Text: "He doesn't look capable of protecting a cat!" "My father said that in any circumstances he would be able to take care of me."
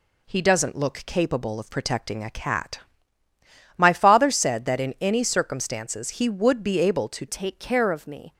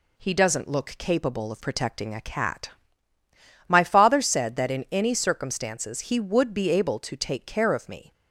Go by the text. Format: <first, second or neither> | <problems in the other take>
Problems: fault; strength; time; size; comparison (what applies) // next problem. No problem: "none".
second | changes voice at "take"; from 7.2 s on; 1.1 s long